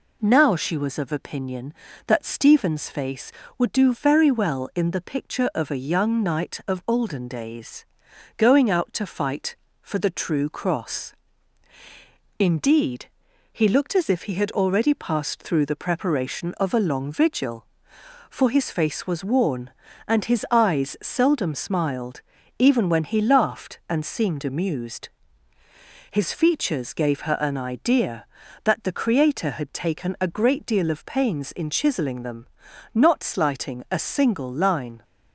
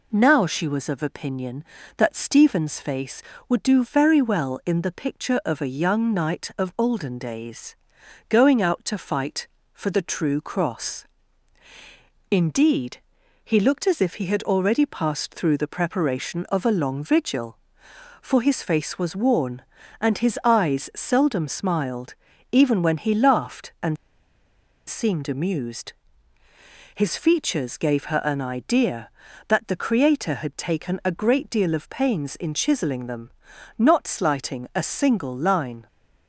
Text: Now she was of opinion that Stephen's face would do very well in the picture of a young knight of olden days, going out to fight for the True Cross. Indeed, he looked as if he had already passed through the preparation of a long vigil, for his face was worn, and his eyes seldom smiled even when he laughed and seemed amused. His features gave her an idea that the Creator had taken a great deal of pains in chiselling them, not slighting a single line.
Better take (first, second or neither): first